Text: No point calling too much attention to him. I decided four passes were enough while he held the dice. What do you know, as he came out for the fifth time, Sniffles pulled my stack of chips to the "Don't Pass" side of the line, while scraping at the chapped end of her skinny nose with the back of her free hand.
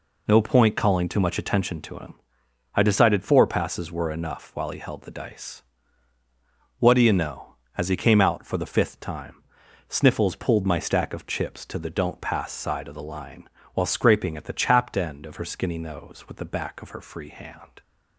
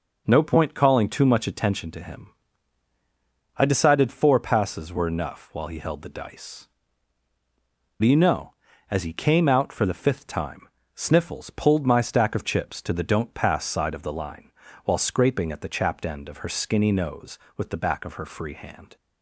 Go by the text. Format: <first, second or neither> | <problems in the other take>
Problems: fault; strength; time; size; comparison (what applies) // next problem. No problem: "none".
first | skips "What"; at 7.3 s